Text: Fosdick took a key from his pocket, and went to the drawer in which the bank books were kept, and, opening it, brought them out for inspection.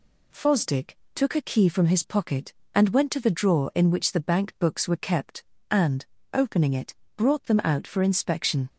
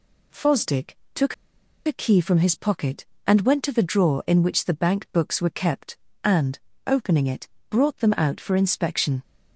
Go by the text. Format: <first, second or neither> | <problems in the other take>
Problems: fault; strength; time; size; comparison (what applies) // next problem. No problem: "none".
first | pauses between "Fosdick" and "took"; slight; at 0.9 s; 0.18 s long; slight in the first // pauses between "took" and "a"; noticeable; at 1.3 s; 0.52 s long